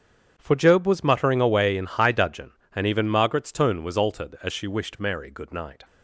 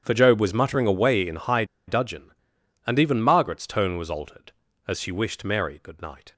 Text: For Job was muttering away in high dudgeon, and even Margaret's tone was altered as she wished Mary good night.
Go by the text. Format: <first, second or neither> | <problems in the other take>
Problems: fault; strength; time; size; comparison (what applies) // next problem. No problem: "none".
first | starts louder than the rest; strong; until 1.0 s; 9 dB; strong in the first // pauses between "high" and "dudgeon"; slight; at 1.6 s; 0.23 s long